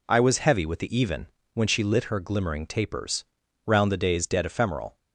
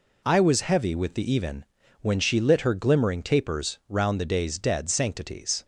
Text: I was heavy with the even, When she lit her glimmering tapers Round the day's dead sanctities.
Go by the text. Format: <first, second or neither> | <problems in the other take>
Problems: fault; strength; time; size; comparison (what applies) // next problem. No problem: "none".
second | pauses between "tapers" and "Round"; at 3.2 s; 0.42 s long // says "ephemeral" for "sanctities"; at 4.4 s